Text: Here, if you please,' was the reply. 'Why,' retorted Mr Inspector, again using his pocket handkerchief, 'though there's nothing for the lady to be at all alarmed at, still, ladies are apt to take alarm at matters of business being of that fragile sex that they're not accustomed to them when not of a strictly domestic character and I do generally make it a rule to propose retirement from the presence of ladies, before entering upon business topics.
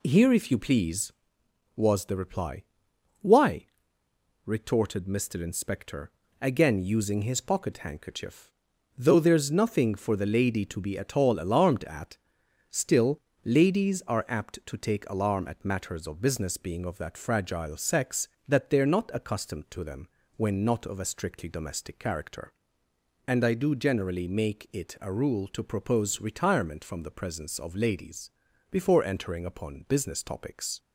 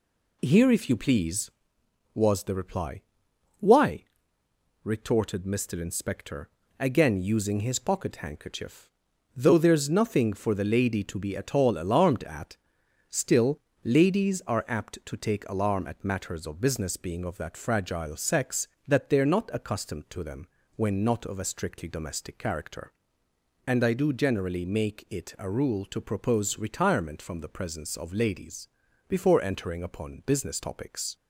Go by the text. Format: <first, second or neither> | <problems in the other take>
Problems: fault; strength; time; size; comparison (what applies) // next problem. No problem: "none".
neither | pauses between "them" and "when"; slight; the same in both